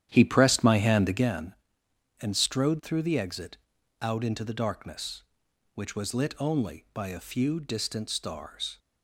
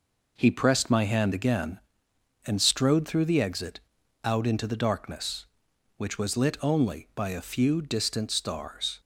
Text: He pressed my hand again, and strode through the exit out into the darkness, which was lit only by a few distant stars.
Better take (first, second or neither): second